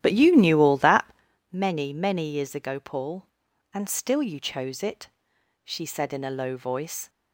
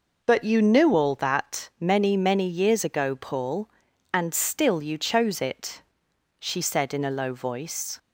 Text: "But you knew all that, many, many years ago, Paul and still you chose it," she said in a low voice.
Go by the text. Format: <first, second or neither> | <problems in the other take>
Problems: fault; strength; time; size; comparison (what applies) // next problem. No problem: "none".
second | starts louder than the rest; strong; until 1.4 s; 11.5 dB